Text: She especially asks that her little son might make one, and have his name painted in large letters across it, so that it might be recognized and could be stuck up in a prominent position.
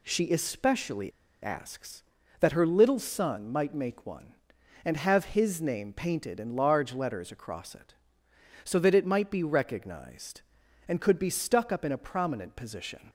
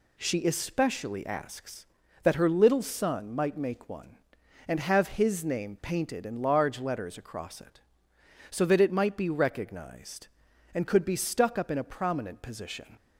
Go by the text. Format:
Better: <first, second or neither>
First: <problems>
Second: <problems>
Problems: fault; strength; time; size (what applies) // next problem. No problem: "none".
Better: second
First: pauses between "especially" and "asks"; slight; at 1.1 s; 0.32 s long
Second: none